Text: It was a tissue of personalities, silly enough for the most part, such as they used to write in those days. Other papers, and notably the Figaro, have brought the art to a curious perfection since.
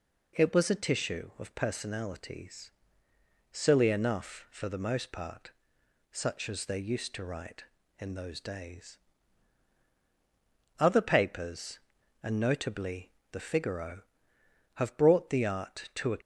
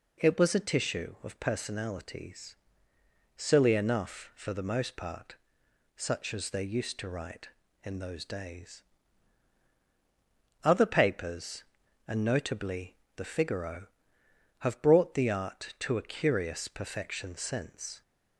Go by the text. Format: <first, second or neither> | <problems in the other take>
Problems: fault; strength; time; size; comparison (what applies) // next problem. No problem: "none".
second | pauses between "notably" and "the"; slight; at 13.1 s; 0.20 s long; slight in the second // stops before "curious perfection since"; at 16.2 s